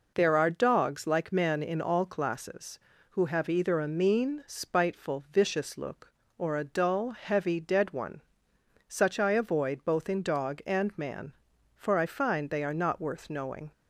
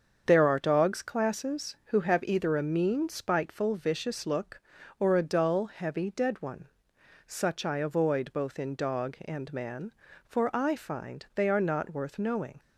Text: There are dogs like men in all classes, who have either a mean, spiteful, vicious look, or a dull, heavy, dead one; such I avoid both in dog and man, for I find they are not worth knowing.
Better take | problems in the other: first | starts louder than the rest; until 1.2 s; 7 dB // skips "like men in all"; at 1.0 s

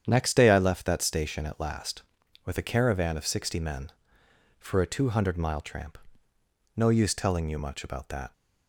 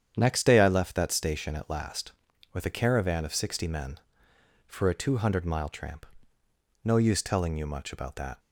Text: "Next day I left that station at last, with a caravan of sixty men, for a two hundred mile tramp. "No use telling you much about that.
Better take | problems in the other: neither | starts louder than the rest; strong; the same in both

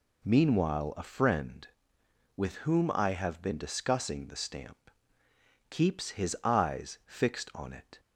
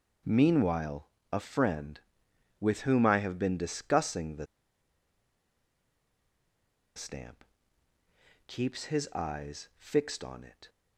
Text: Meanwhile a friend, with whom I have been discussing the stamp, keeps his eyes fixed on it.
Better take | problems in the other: first | pauses between "Meanwhile" and "a"; slight; at 1.0 s; 0.24 s long // pauses between "the" and "stamp"; strong; at 4.4 s; 2.5 s long

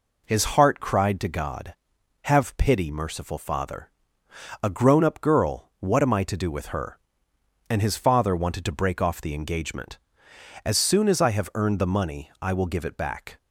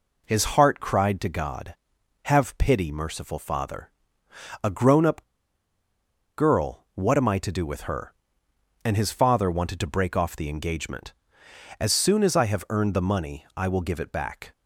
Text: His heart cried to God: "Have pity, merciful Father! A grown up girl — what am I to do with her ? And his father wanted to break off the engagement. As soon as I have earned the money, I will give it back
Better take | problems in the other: first | pauses between "up" and "girl"; at 5.2 s; 1.1 s long

